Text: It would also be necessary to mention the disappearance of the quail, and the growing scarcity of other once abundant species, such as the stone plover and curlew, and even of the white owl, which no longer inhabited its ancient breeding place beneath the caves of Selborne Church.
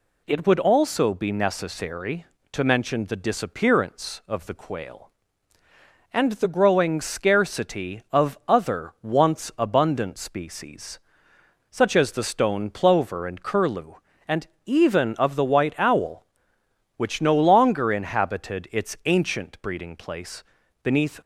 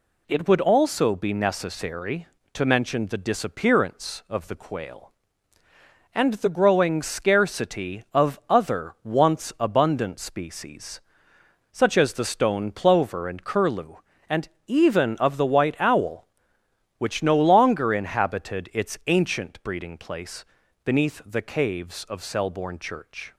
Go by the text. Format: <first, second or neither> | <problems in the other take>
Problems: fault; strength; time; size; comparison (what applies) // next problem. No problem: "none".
second | pauses between "and" and "even"; slight; at 14.4 s; 0.18 s long; slight in the second // pauses between "place" and "beneath"; at 20.4 s; 0.42 s long; also in the second // stops before "the caves of Selborne Church"; at 21.2 s